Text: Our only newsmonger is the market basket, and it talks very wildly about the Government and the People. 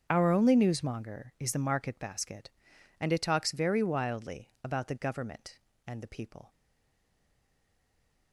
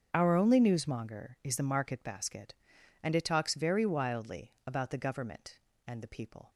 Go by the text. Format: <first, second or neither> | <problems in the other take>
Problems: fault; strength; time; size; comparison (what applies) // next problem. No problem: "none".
second | starts louder than the rest; until 1.1 s; 7 dB; also in the second // stays silent after the last word; noticeable; from 6.4 s on; 1.9 s long